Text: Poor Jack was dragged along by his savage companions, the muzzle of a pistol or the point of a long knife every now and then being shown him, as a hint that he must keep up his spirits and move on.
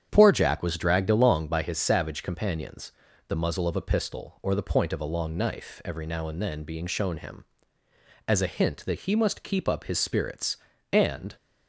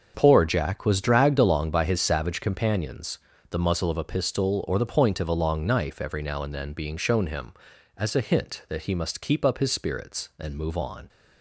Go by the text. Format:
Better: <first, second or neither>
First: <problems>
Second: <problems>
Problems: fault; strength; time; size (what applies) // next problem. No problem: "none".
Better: second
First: starts louder than the rest; strong; until 1.1 s; 8.5 dB // stops before "move on"; at 11.3 s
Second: starts louder than the rest; until 1.1 s; 6.5 dB